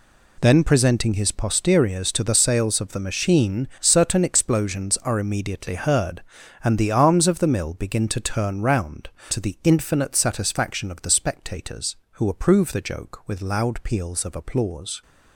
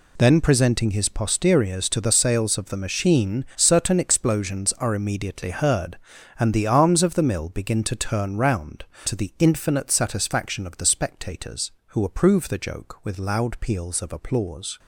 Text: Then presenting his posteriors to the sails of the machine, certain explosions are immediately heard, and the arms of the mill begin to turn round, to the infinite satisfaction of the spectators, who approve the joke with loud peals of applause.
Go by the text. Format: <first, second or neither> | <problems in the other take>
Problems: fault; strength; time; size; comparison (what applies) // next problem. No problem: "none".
neither | none